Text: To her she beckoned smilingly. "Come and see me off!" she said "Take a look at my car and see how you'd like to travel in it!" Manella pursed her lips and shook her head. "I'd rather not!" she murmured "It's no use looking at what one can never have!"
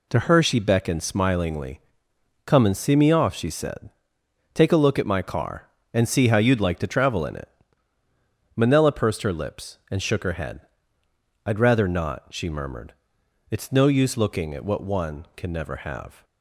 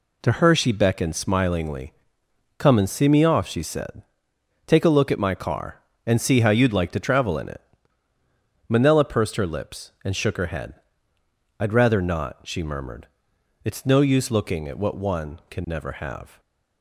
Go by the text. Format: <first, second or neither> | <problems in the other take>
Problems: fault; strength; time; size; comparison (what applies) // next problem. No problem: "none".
neither | pauses between "said" and "Take"; noticeable; the same in both // pauses between "murmured" and "It's"; noticeable; the same in both